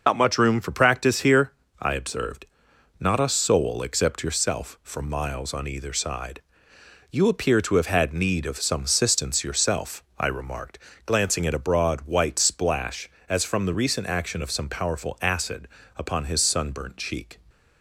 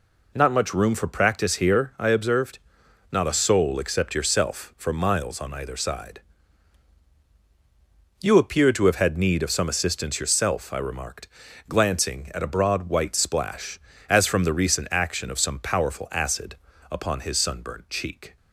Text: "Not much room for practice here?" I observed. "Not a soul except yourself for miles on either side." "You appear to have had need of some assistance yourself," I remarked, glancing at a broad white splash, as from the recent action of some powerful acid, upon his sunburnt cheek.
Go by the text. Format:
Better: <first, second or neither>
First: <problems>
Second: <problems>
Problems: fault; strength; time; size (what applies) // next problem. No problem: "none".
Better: second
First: loses the start of "Not"; at 0.0 s; 90 ms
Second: none